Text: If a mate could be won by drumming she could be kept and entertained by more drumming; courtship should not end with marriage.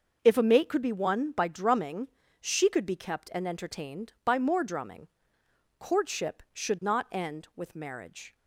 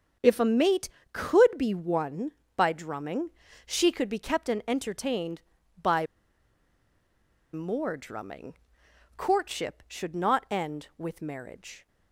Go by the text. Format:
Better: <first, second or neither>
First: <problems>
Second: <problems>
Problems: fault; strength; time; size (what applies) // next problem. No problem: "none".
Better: first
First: starts louder than the rest; until 1.2 s; 6 dB // pauses between "drumming" and "she"; slight; at 2.0 s; 0.32 s long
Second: starts louder than the rest; until 1.4 s; 7 dB // pauses between "drumming" and "she"; slight; at 3.3 s; 0.36 s long // pauses between "by" and "more"; strong; at 6.0 s; 1.4 s long